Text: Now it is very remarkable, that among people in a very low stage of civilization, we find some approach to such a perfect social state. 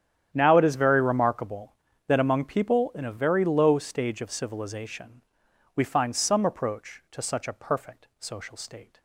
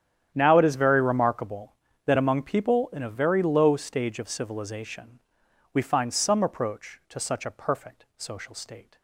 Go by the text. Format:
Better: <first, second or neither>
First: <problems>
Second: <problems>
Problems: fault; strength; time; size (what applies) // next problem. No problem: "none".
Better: neither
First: starts louder than the rest; strong; until 1.3 s; 10 dB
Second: starts louder than the rest; strong; until 1.3 s; 10 dB